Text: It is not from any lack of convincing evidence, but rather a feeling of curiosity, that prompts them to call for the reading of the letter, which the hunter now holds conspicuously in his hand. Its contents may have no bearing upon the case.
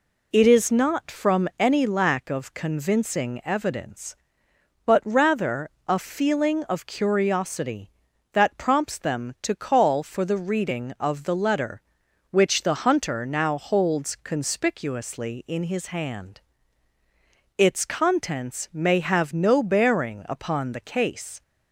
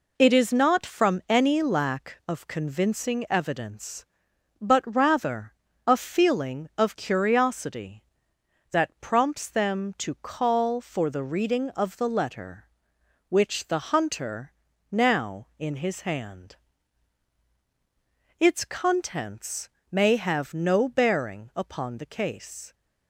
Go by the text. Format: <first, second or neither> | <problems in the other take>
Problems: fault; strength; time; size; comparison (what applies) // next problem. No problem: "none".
first | pauses between "rather" and "a"; slight; at 5.5 s; 0.34 s long; slight in the first // pauses between "hunter" and "now"; slight; at 14.5 s; 0.36 s long // skips "holds conspicuously"; at 15.5 s // pauses between "contents" and "may"; slight; at 19.6 s; 0.24 s long